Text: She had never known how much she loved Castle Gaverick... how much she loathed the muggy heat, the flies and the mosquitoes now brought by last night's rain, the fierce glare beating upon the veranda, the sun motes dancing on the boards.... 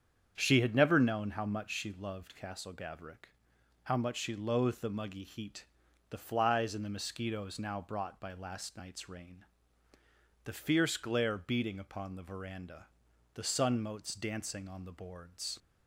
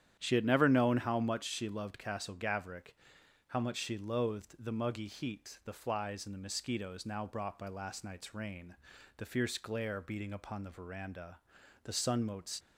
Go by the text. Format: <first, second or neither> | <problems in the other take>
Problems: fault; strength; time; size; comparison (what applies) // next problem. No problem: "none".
first | starts louder than the rest; strong; until 1.2 s; 10 dB; strong in the first // stops before "dancing on the boards"; at 12.5 s